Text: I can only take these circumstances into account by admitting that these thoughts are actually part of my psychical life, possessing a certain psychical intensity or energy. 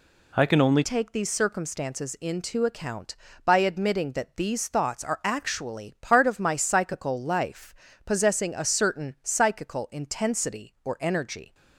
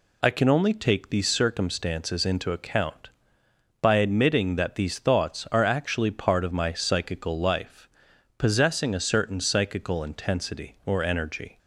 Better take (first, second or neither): second